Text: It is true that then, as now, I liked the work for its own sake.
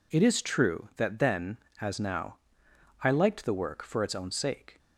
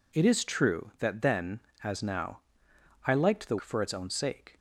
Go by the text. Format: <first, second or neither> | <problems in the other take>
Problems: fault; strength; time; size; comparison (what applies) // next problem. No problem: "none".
first | skips "work"; at 3.5 s